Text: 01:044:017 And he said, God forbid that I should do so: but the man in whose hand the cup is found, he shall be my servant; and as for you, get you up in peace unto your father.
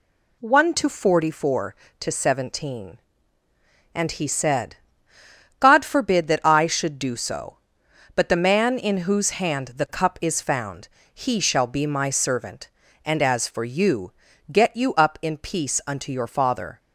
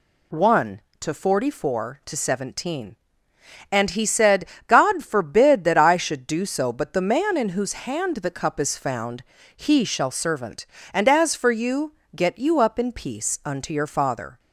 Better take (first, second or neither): first